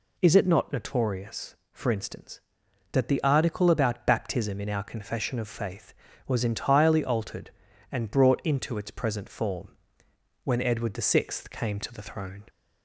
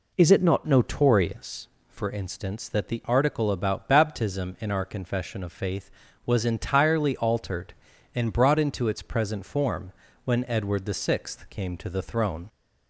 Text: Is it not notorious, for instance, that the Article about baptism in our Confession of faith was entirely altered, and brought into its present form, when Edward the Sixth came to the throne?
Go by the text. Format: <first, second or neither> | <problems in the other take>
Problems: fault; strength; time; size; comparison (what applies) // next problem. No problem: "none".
first | changes voice at "notorious"; from 0.6 s on; 11.8 s long